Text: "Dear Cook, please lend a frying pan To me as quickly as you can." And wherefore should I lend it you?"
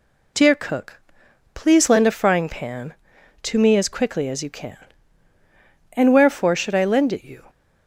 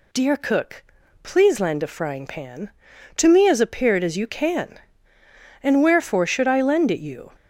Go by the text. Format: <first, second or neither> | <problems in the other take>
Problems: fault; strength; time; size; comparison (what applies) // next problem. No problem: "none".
first | says "appeared" for "quickly"; at 3.6 s